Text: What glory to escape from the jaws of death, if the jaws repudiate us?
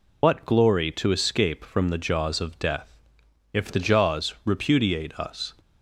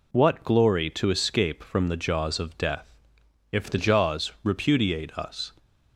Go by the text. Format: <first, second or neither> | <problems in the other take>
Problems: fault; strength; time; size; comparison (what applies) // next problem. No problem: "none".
second | loses the start of "What"; at 0.2 s; 90 ms